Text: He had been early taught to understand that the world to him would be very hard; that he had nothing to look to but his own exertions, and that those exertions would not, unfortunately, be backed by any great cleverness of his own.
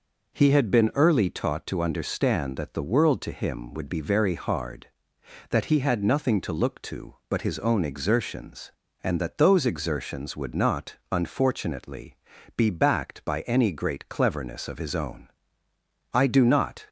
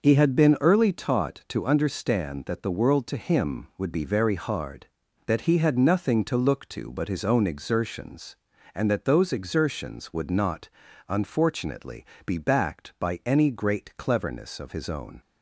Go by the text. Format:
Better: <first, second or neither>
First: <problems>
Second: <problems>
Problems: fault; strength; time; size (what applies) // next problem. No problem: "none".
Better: second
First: goes on to say "I do not"; noticeable; from 16.1 s on; 0.74 s long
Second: none